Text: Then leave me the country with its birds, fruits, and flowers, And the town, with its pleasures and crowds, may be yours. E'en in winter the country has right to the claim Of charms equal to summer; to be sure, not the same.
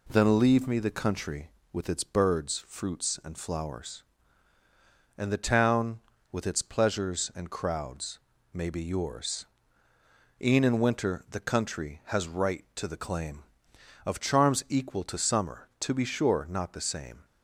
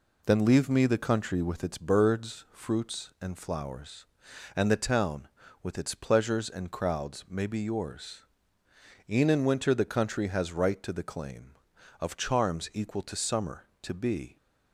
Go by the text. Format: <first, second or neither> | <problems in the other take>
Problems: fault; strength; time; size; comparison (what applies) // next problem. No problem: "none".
first | stops before "sure not the same"; at 14.3 s